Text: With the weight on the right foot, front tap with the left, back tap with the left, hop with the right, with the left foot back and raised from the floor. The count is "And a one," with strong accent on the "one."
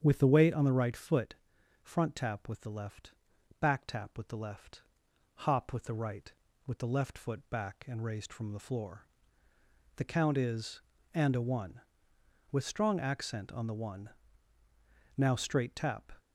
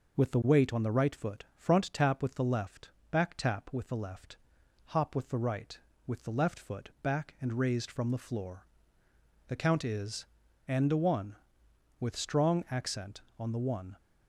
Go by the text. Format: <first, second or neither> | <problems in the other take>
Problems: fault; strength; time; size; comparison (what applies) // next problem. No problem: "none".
second | starts louder than the rest; strong; until 1.0 s; 8 dB // goes on to say "Now straight tap"; noticeable; from 15.1 s on; 0.96 s long